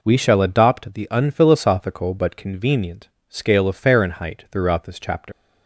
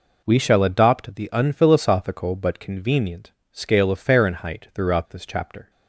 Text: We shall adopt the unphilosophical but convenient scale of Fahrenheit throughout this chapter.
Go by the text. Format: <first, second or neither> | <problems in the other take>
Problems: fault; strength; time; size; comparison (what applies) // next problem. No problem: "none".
second | pauses between "convenient" and "scale"; slight; at 3.0 s; 0.18 s long; slight in the second // leaves "chapter" unfinished; at 5.3 s; 115 ms